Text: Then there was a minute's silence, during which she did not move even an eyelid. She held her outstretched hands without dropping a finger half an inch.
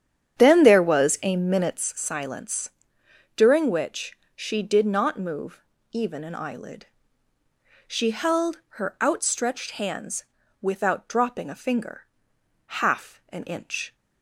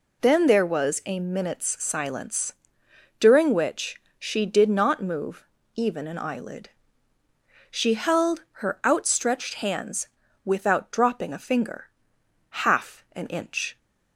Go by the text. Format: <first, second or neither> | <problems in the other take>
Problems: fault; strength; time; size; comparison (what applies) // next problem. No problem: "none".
second | starts louder than the rest; strong; until 1.8 s; 9 dB // pauses between "which" and "she"; slight; at 4.1 s; 0.18 s long; slight in the second // pauses between "move" and "even"; slight; at 5.6 s; 0.32 s long; slight in the second // pauses between "hands" and "without"; slight; at 10.2 s; 0.36 s long; slight in the second // pauses between "finger" and "half"; noticeable; at 12.0 s; 0.60 s long; noticeable in the second